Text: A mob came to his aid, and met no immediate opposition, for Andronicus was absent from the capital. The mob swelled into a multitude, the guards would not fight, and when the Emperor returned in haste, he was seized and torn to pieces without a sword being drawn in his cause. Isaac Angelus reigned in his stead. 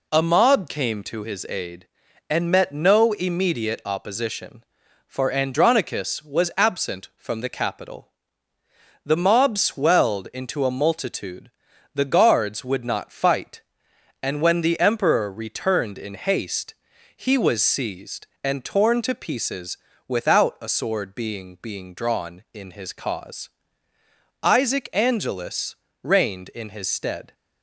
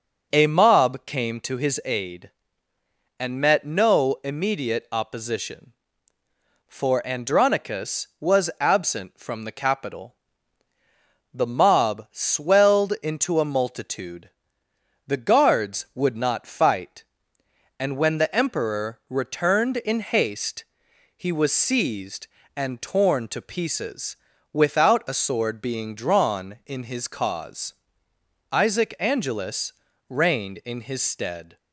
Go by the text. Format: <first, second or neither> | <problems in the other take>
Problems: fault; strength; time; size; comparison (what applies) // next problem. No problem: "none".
second | pauses between "pieces" and "without"; slight; at 19.7 s; 0.32 s long; also in the second // says "being" twice; at 21.6 s // pauses between "Angelus" and "reigned"; slight; at 25.7 s; 0.26 s long; slight in the second